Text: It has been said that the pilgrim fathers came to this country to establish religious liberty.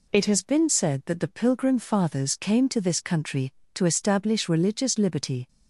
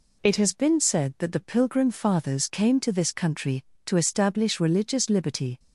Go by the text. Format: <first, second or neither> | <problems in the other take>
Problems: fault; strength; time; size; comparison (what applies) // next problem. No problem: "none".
neither | none